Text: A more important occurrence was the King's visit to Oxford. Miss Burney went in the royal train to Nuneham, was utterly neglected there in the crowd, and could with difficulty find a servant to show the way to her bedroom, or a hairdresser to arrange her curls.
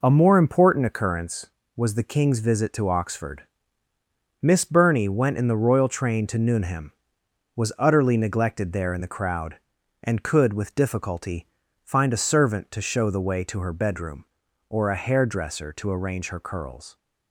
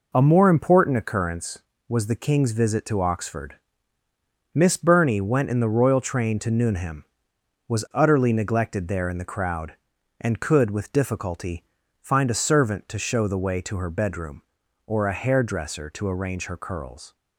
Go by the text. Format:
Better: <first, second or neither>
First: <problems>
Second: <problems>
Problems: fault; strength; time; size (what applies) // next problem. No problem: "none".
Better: neither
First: pauses between "difficulty" and "find"; slight; at 11.4 s; 0.34 s long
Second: pauses between "difficulty" and "find"; slight; at 11.6 s; 0.34 s long